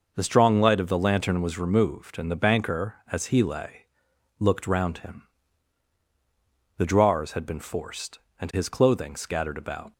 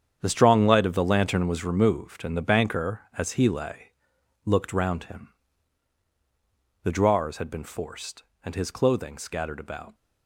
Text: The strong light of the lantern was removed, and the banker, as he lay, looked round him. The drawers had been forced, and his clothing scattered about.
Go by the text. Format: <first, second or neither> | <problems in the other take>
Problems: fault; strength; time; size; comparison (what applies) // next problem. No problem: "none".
first | gets quieter; strong; throughout; 11.5 dB